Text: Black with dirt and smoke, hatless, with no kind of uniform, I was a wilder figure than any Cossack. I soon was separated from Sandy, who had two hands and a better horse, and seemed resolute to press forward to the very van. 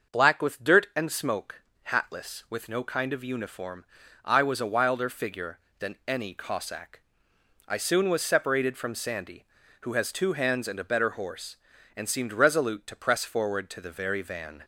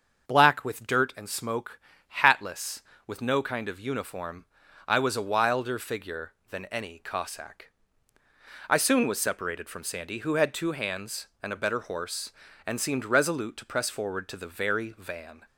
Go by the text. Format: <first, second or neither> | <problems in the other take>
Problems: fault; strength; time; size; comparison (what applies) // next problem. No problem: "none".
second | starts louder than the rest; until 1.2 s; 6.5 dB; also in the second // says "has" for "had"; at 9.9 s